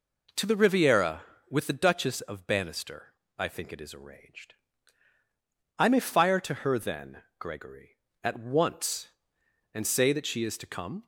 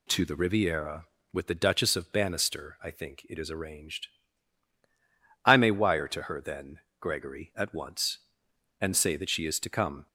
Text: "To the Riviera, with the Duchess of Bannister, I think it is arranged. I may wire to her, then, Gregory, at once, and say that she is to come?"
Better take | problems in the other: second | says "fire" for "wire"; at 5.9 s

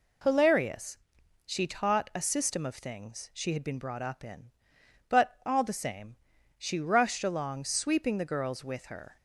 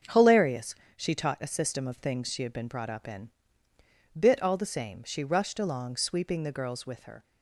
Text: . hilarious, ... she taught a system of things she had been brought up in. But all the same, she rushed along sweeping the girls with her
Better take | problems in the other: first | starts louder than the rest; until 1.2 s; 6.5 dB // says "Bit" for "But"; at 4.1 s

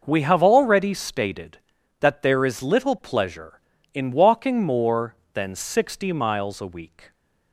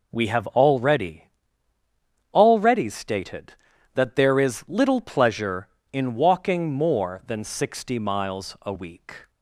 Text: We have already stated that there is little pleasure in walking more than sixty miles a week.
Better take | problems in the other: first | says "already" twice; at 2.3 s

